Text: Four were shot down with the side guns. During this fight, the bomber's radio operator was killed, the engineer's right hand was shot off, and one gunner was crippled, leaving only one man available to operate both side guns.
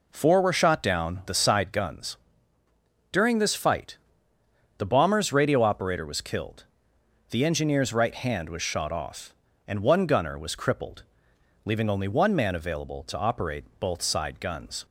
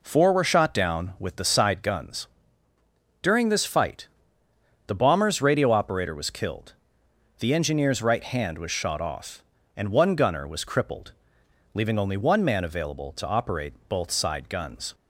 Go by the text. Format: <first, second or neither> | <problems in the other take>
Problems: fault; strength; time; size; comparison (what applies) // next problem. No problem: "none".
second | skips "with"; at 1.2 s